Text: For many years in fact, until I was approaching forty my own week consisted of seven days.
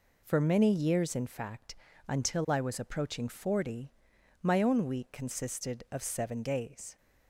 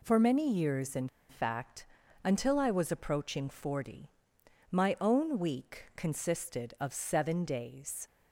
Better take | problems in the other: first | pauses between "in" and "fact"; slight; at 1.0 s; 0.22 s long // pauses between "forty" and "my"; noticeable; at 4.1 s; 0.58 s long; noticeable in the first

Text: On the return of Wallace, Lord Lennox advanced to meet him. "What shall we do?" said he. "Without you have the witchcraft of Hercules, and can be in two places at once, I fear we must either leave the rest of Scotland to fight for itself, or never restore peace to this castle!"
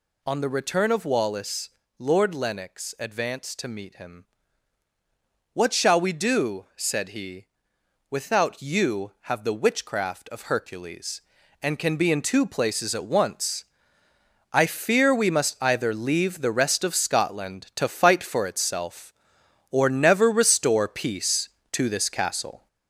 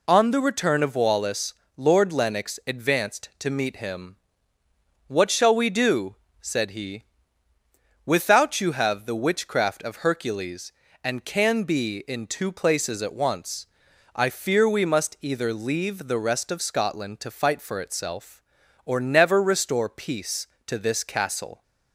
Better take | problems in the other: second | gets louder; noticeable; throughout; 5 dB

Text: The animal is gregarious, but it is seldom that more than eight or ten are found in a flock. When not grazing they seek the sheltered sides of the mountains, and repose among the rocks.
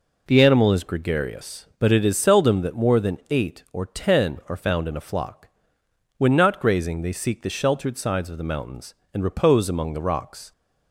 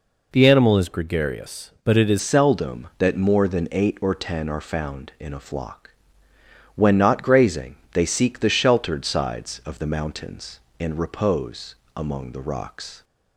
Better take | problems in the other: first | changes voice at "seldom"; from 2.1 s on; 10.9 s long // pauses between "grazing" and "they"; slight; at 7.7 s; 0.16 s long // pauses between "repose" and "among"; slight; at 11.7 s; 0.20 s long

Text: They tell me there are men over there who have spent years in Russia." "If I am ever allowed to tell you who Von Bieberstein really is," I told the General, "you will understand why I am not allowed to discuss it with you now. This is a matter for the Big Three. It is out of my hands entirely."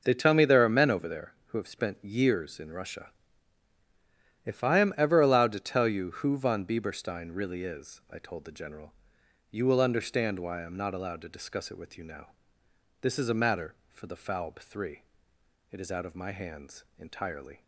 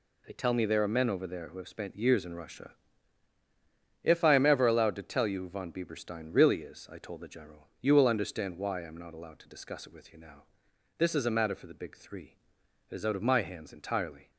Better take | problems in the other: second | says "Falb" for "Big"; at 14.1 s // pauses between "hands" and "entirely"; slight; at 16.8 s; 0.16 s long

